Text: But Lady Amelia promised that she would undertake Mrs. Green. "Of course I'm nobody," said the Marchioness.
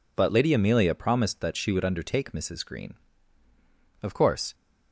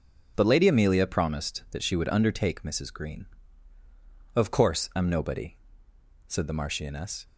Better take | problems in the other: second | stops before "I'm nobody said the Marchioness"; at 4.5 s

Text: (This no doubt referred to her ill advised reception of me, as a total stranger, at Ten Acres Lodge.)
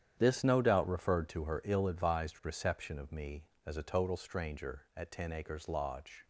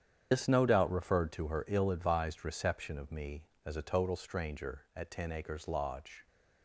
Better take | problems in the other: first | loses the start of "This"; at 0.3 s; 75 ms // starts louder than the rest; strong; until 1.3 s; 8.5 dB; strong in the first

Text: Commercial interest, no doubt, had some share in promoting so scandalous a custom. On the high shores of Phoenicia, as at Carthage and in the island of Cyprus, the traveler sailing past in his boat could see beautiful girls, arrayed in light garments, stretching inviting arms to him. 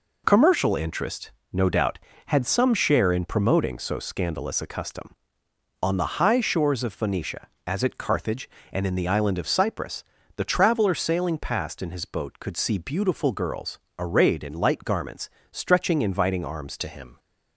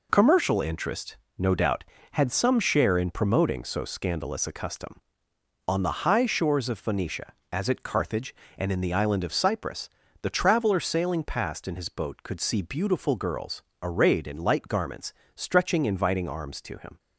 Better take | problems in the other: second | changes voice at "to"; from 16.7 s on; 0.4 s long

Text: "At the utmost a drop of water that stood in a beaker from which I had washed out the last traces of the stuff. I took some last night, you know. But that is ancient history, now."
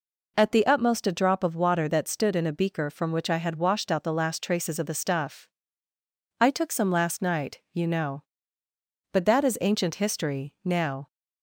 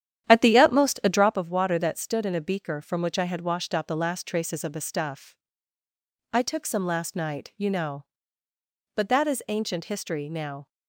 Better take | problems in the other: first | starts louder than the rest; strong; until 1.4 s; 10.5 dB

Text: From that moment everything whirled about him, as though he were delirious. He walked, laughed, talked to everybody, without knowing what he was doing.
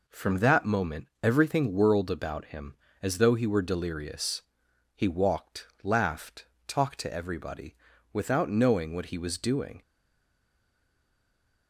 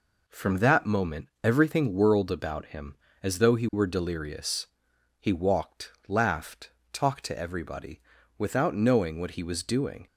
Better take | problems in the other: second | stays silent after the last word; noticeable; from 9.8 s on; 1.8 s long

